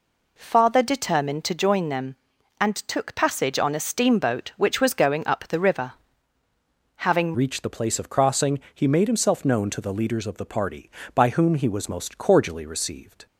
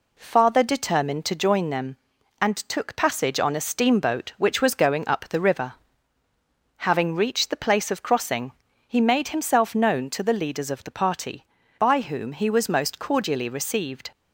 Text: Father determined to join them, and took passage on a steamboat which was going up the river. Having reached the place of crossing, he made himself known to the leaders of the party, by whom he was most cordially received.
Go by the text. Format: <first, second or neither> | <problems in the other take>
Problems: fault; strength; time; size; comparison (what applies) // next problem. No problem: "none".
second | changes voice at "reached"; from 7.3 s on; 5.9 s long